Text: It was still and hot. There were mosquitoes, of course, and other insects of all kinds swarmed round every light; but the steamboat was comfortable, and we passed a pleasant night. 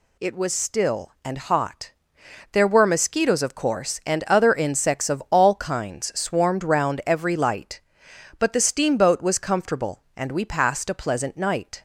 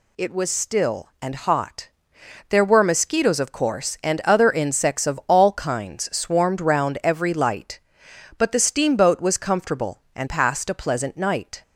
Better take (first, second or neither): first